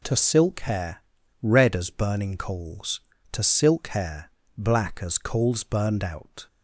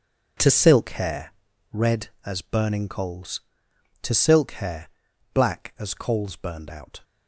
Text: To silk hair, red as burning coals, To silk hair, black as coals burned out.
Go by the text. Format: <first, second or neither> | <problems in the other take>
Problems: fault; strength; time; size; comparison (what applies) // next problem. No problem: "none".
first | gets quieter; strong; throughout; 12 dB